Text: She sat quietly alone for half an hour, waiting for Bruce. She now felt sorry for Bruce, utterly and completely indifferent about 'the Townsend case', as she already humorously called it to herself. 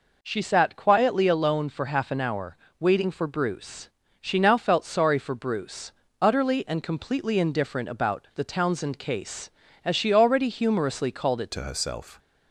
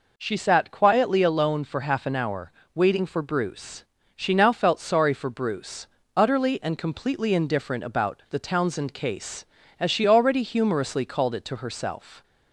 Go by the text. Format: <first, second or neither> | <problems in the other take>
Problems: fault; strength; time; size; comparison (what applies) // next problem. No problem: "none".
second | changes voice at "to"; from 11.5 s on; 0.6 s long